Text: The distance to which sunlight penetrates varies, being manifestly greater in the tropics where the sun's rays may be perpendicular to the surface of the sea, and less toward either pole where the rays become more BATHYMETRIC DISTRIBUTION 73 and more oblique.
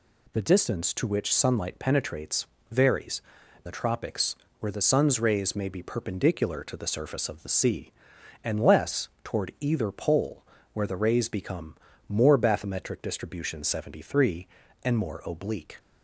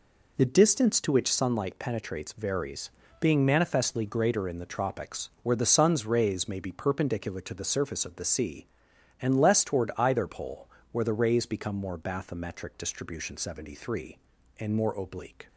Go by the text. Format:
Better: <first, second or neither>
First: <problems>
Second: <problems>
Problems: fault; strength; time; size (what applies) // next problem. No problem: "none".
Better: second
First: pauses between "penetrates" and "varies"; slight; at 2.4 s; 0.24 s long // skips "being manifestly greater in"; at 3.4 s // pauses between "tropics" and "where"; slight; at 4.3 s; 0.24 s long // pauses between "pole" and "where"; slight; at 10.4 s; 0.30 s long // pauses between "become" and "more"; slight; at 11.7 s; 0.34 s long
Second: pauses between "pole" and "where"; slight; at 10.6 s; 0.24 s long